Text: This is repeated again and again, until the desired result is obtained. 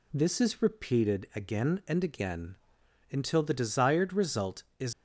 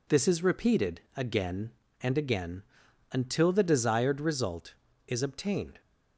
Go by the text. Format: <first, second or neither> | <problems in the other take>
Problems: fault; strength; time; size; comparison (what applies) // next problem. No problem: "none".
second | stops before "obtained"; at 4.9 s